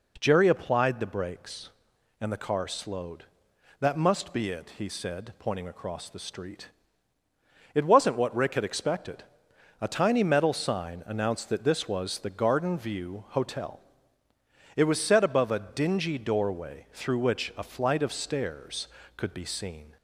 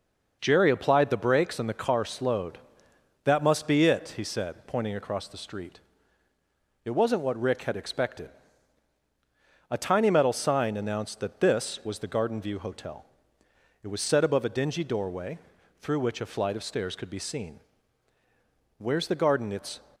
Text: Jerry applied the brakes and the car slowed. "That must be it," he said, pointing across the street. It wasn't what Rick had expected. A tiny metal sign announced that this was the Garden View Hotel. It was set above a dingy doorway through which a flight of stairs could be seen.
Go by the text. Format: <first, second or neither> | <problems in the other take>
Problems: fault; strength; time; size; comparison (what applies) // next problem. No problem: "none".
first | pauses between "doorway" and "through"; at 15.3 s; 0.42 s long // goes on to say "Where's the garden it's"; noticeable; from 18.7 s on; 1.0 s long